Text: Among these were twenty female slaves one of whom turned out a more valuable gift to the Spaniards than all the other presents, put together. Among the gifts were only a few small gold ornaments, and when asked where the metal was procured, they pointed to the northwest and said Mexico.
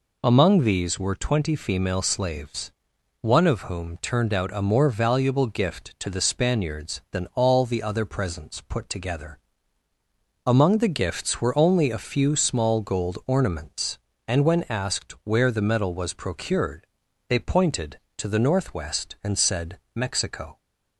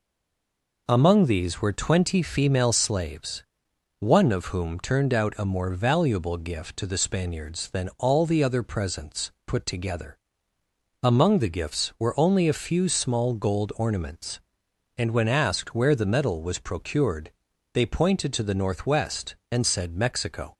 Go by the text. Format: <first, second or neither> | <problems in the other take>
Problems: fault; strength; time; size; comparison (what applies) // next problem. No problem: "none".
first | stays silent before the first word; slight; until 0.8 s; 0.8 s long // pauses between "slaves" and "one"; noticeable; at 3.4 s; 0.56 s long; noticeable in the first